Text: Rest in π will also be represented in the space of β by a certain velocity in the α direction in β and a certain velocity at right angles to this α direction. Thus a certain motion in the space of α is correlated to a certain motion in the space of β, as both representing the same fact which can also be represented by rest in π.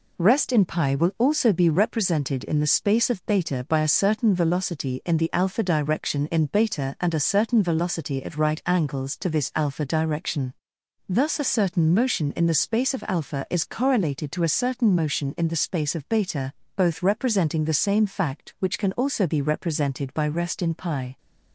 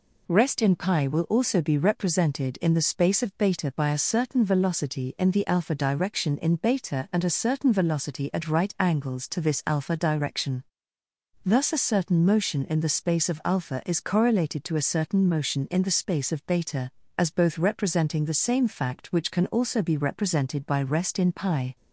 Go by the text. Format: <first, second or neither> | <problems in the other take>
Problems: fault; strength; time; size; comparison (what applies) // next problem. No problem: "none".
second | skips "as"; at 16.6 s